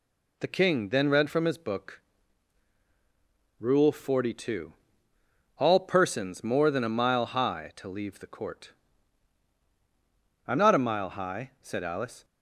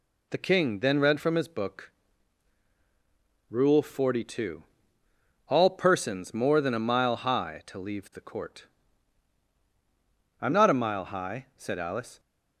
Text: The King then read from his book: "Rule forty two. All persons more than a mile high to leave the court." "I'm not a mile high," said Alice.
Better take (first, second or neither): neither